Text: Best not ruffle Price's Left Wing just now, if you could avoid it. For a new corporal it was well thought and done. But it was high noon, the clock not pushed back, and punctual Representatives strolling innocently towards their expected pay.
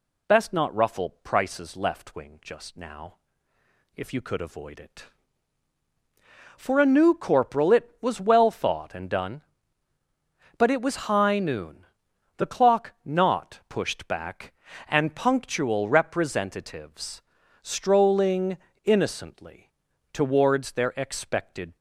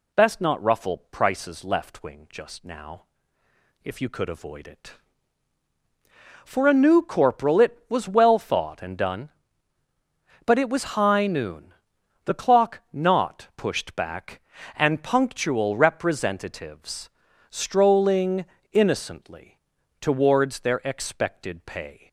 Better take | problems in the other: second | pauses between "Representatives" and "strolling"; at 17.1 s; 0.42 s long; also in the second // pauses between "strolling" and "innocently"; slight; at 18.5 s; 0.28 s long; slight in the second // pauses between "innocently" and "towards"; at 19.7 s; 0.40 s long; also in the second // stops before "pay"; at 21.7 s

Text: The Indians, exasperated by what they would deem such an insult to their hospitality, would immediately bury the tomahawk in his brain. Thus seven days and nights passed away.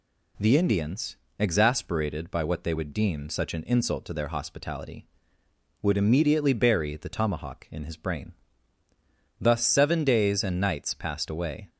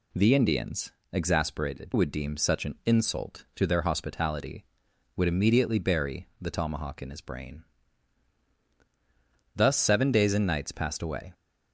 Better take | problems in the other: first | skips "by what they"; at 1.9 s

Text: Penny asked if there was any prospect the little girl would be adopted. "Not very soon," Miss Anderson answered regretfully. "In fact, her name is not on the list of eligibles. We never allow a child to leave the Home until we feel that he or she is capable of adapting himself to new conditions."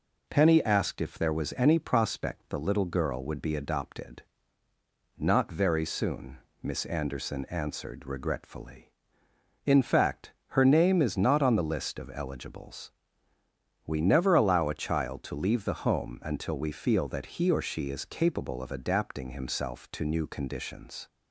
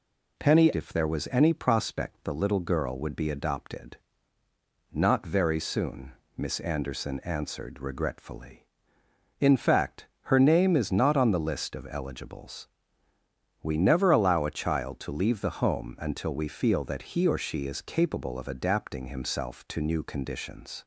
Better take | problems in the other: first | skips "asked"; at 0.7 s

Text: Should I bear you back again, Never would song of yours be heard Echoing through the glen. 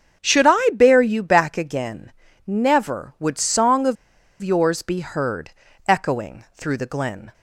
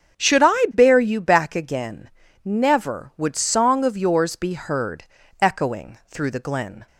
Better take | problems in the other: second | starts louder than the rest; until 1.2 s; 6.5 dB; strong in the second // pauses between "of" and "yours"; noticeable; at 3.9 s; 0.47 s long // pauses between "heard" and "Echoing"; at 5.5 s; 0.38 s long; also in the second

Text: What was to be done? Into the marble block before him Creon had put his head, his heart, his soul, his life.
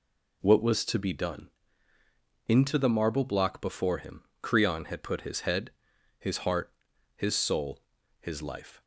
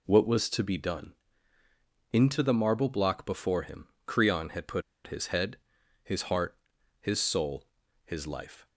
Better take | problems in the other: first | pauses between "him" and "Creon"; slight; at 3.8 s; 0.18 s long; slight in the first // pauses between "put" and "his"; slight; at 4.8 s; 0.24 s long

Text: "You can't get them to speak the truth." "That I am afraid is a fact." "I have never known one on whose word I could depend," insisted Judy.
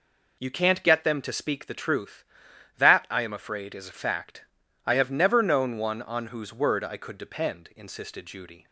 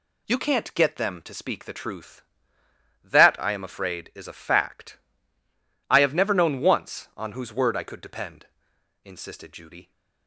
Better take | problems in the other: first | says "once" for "one"; at 6.6 s

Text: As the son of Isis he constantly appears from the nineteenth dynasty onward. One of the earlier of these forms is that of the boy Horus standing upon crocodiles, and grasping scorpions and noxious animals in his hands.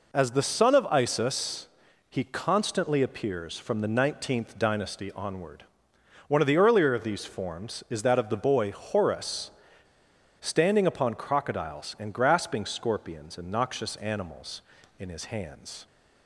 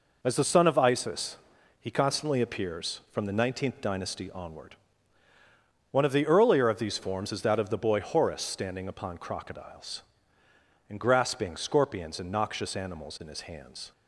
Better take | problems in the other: second | pauses between "Isis" and "he"; at 1.6 s; 0.44 s long; also in the second // pauses between "Horus" and "standing"; noticeable; at 9.5 s; 0.88 s long

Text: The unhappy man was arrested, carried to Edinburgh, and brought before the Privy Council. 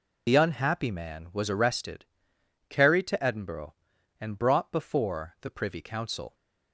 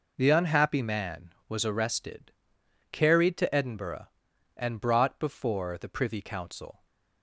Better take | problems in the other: second | loses the start of "The"; at 0.2 s; 65 ms

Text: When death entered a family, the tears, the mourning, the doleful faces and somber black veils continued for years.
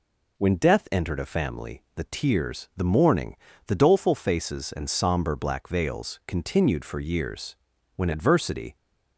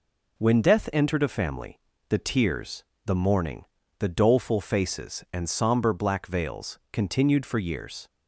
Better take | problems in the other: second | goes on to say "When adversity"; noticeable; from 7.9 s on; 0.80 s long

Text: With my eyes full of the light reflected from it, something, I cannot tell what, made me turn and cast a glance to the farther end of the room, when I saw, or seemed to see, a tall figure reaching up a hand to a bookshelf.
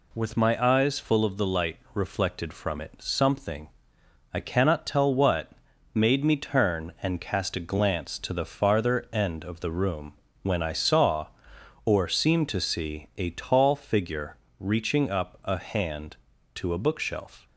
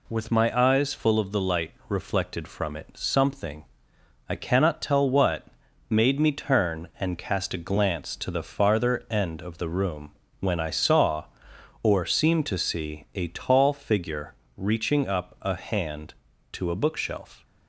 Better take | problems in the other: neither | pauses between "light" and "reflected"; slight; the same in both // pauses between "figure" and "reaching"; slight; the same in both

